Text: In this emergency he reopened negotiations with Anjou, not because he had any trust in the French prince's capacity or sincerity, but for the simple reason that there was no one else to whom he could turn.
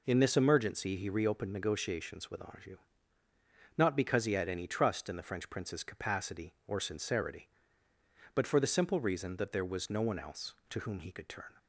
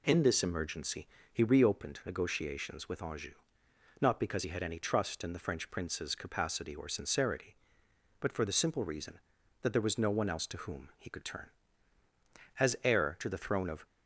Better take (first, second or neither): first